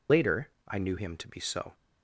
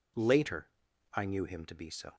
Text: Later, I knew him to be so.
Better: second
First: loses the start of "Later"; at 0.0 s; 115 ms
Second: none

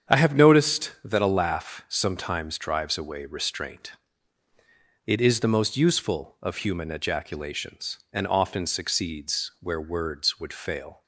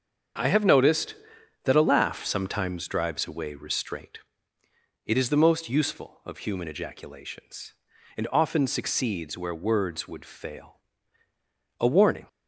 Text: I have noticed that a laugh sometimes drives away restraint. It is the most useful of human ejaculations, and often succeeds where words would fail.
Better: first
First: starts louder than the rest; strong; until 1.1 s; 8 dB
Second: starts louder than the rest; until 1.8 s; 7 dB // goes on to say "A warning"; slight; from 11.8 s on; 0.46 s long

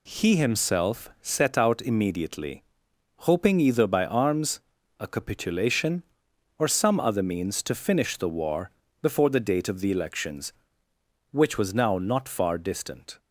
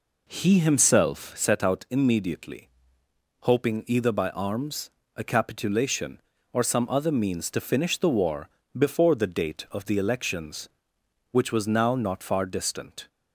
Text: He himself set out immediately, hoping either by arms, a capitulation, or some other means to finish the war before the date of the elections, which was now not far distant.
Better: first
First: pauses between "war" and "before"; slight; at 8.7 s; 0.32 s long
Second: starts louder than the rest; until 1.5 s; 4 dB // pauses between "war" and "before"; slight; at 8.4 s; 0.28 s long

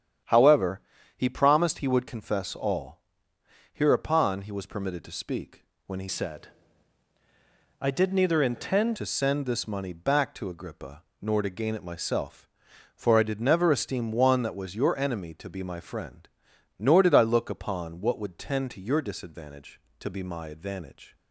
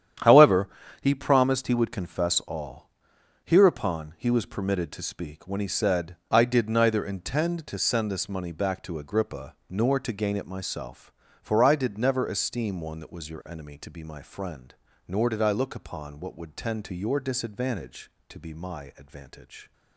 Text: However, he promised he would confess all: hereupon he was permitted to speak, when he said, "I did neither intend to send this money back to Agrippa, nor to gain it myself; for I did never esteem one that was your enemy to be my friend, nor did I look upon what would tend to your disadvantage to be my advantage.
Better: second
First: starts louder than the rest; strong; until 1.6 s; 9.5 dB // changes voice from "said" to "intend"; from 6.0 to 8.9 s; 2.9 s long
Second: starts louder than the rest; strong; until 1.5 s; 9.5 dB

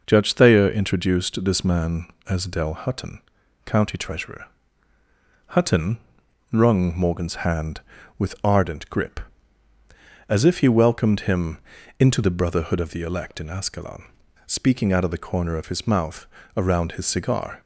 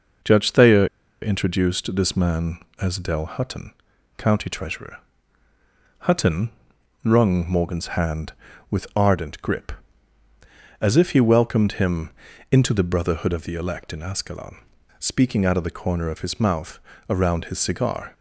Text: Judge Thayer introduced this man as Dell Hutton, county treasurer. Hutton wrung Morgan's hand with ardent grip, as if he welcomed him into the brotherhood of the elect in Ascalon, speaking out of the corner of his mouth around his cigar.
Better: first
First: pauses between "Hutton" and "wrung"; noticeable; at 5.9 s; 0.52 s long // pauses between "him" and "into"; at 11.5 s; 0.40 s long // pauses between "mouth" and "around"; slight; at 16.2 s; 0.30 s long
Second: pauses between "Thayer" and "introduced"; at 0.8 s; 0.36 s long // pauses between "Hutton" and "wrung"; noticeable; at 6.5 s; 0.52 s long // pauses between "him" and "into"; at 12.1 s; 0.40 s long // pauses between "mouth" and "around"; slight; at 16.7 s; 0.30 s long

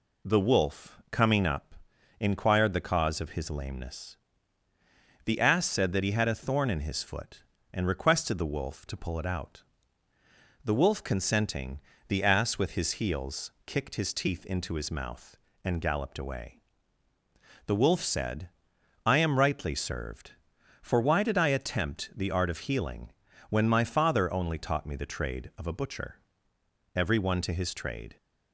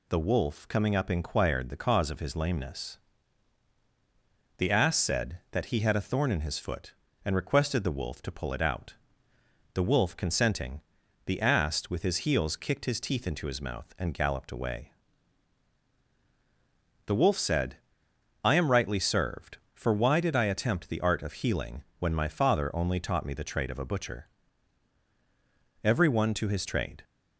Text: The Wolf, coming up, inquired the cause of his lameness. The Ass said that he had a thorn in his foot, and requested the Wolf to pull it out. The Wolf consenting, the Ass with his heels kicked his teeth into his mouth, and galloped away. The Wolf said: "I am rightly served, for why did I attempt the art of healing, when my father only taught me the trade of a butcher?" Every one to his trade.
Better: neither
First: none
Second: none

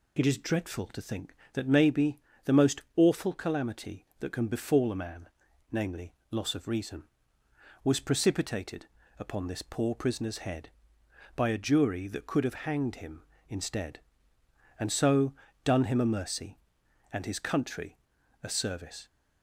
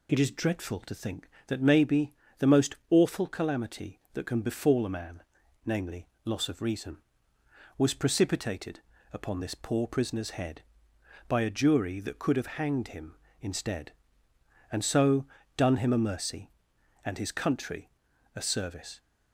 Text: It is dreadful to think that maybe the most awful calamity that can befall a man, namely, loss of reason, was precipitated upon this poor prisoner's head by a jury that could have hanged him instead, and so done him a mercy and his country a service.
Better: neither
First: pauses between "maybe" and "the"; slight; at 2.2 s; 0.24 s long // pauses between "most" and "awful"; slight; at 2.8 s; 0.16 s long // pauses between "precipitated" and "upon"; slight; at 8.8 s; 0.32 s long // pauses between "so" and "done"; slight; at 15.3 s; 0.30 s long // pauses between "country" and "a"; at 17.9 s; 0.44 s long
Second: pauses between "maybe" and "the"; slight; at 2.1 s; 0.24 s long // pauses between "most" and "awful"; slight; at 2.7 s; 0.16 s long // pauses between "precipitated" and "upon"; slight; at 8.8 s; 0.32 s long // pauses between "so" and "done"; slight; at 15.2 s; 0.30 s long // pauses between "country" and "a"; at 17.9 s; 0.44 s long

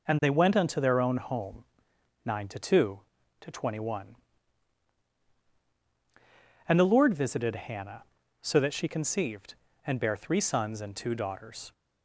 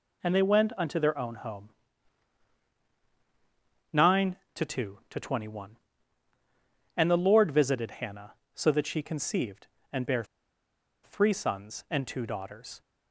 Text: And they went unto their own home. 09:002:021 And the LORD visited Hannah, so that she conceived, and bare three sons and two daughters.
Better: first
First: none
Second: pauses between "bare" and "three"; noticeable; at 10.2 s; 0.79 s long

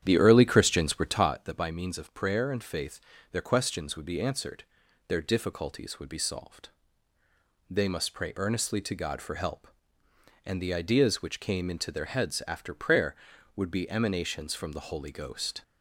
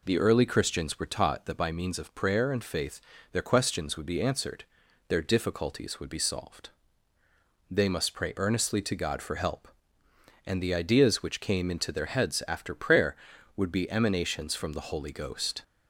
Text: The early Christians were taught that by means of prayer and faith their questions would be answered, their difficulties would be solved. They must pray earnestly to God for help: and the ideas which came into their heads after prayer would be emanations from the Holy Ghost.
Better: second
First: starts louder than the rest; strong; until 1.3 s; 9.5 dB // pauses between "faith" and "their"; slight; at 3.0 s; 0.30 s long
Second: pauses between "faith" and "their"; slight; at 3.0 s; 0.30 s long

